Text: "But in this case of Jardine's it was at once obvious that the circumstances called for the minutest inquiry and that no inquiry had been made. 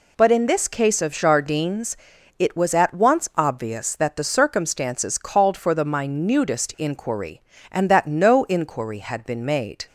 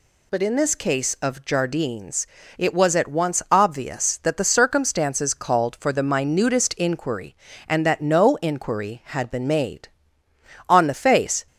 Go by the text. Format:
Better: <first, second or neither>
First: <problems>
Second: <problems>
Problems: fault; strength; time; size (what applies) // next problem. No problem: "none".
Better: first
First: pauses between "Jardine's" and "it"; at 1.9 s; 0.42 s long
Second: pauses between "Jardine's" and "it"; slight; at 2.2 s; 0.32 s long // goes on to say "On the face"; noticeable; from 10.6 s on; 0.78 s long